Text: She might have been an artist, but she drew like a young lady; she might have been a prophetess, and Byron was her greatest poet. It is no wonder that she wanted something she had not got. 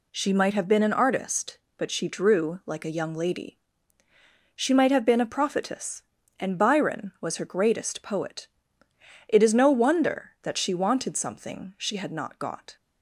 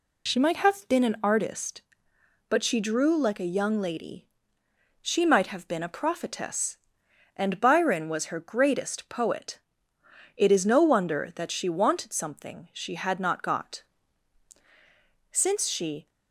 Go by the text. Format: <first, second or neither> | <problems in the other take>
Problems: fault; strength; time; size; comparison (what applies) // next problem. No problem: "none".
first | goes on to say "Since she"; noticeable; from 15.3 s on; 0.78 s long